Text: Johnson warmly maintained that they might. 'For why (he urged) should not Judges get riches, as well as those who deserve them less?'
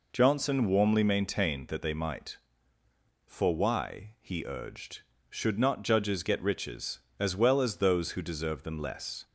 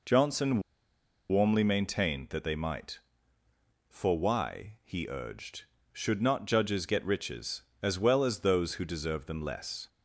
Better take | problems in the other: first | pauses between "Johnson" and "warmly"; noticeable; at 0.6 s; 0.69 s long

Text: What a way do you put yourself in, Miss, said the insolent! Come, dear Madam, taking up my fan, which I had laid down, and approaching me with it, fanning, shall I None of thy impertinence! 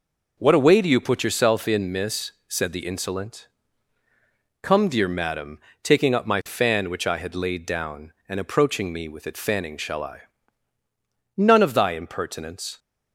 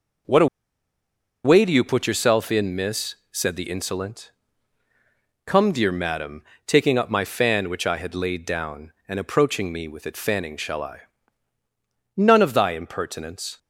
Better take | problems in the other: first | pauses between "a" and "way"; at 0.4 s; 0.98 s long // pauses between "I" and "None"; at 11.0 s; 1.1 s long; also in the first

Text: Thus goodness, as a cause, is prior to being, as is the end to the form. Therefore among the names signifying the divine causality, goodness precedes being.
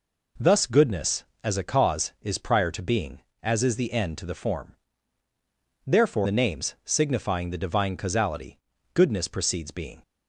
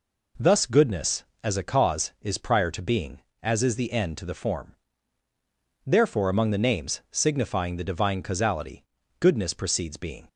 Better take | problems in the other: second | skips "among"; at 6.2 s

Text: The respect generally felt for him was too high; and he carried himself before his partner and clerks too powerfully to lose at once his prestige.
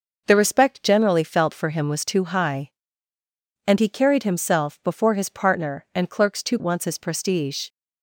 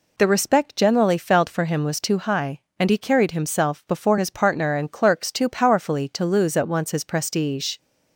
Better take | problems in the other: second | skips "powerfully to lose at"; at 6.5 s

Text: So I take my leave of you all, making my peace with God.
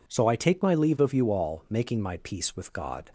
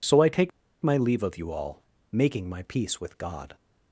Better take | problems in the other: first | pauses between "take" and "my"; slight; at 0.5 s; 0.32 s long

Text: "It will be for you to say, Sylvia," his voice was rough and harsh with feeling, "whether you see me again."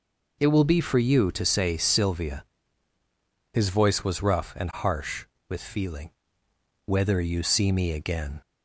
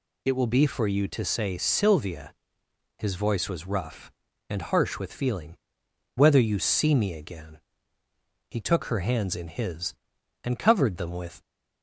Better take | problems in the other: first | goes on to say "He took her hands in his and covered them with"; strong; from 8.5 s on; 2.9 s long

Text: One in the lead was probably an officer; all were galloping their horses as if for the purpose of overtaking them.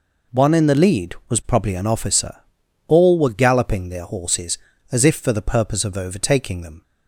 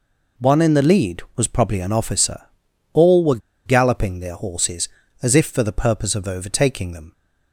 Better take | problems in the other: first | pauses between "were" and "galloping"; slight; at 3.3 s; 0.28 s long

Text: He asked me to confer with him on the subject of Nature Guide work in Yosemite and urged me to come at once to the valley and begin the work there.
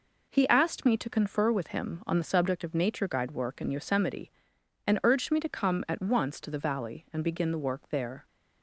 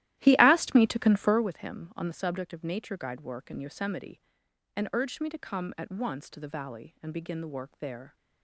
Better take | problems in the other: first | starts louder than the rest; strong; until 1.6 s; 14.5 dB

